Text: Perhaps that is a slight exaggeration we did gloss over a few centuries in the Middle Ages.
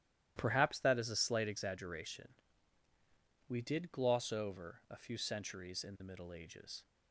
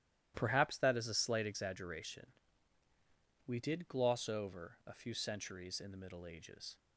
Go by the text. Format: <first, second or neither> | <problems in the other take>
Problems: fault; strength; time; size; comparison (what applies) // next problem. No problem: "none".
neither | starts louder than the rest; strong; the same in both // pauses between "exaggeration" and "we"; the same in both